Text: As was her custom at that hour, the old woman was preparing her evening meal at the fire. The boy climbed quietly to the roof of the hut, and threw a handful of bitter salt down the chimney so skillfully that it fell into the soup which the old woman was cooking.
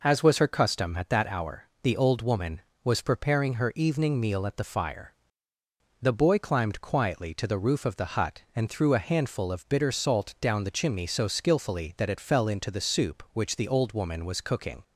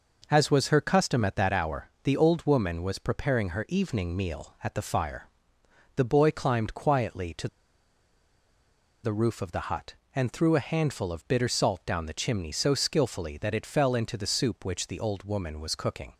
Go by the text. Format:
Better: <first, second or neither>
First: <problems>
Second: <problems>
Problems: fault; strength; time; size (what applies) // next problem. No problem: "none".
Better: first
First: none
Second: pauses between "to" and "the"; strong; at 7.4 s; 1.5 s long